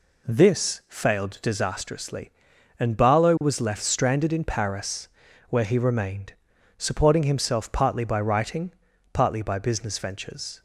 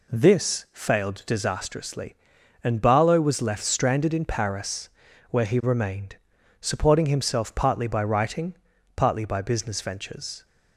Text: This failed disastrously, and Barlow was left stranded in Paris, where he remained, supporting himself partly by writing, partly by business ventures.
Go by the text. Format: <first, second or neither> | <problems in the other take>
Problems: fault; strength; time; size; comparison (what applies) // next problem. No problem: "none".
neither | none